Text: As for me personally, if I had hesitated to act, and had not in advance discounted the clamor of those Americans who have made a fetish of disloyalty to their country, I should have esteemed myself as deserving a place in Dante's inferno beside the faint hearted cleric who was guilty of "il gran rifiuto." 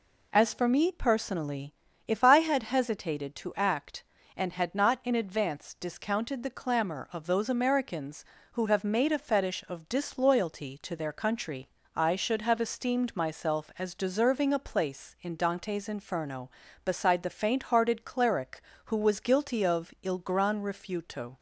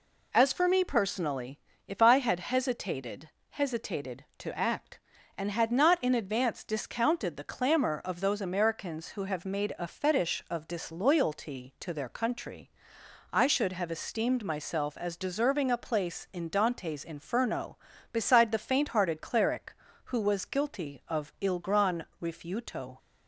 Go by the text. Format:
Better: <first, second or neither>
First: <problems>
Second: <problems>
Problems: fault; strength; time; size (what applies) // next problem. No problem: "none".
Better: first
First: none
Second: says "hesitated" twice; at 3.4 s // pauses between "gran" and "rifiuto"; slight; at 22.0 s; 0.18 s long